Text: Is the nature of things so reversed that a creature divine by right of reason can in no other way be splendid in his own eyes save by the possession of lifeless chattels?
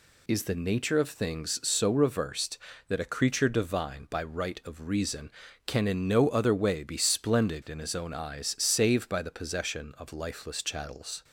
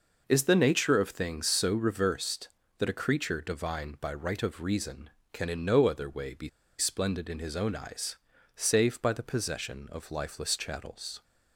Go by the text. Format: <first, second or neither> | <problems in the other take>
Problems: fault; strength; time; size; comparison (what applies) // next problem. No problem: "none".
first | pauses between "be" and "splendid"; slight; at 6.4 s; 0.30 s long // pauses between "eyes" and "save"; at 8.1 s; 0.38 s long